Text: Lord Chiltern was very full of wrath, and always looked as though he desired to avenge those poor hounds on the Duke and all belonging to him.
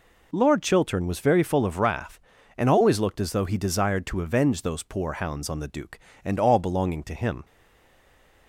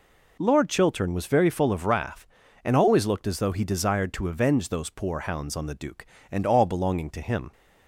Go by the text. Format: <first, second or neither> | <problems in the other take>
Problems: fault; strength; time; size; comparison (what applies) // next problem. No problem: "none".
second | stays silent after the last word; from 7.4 s on; 1.0 s long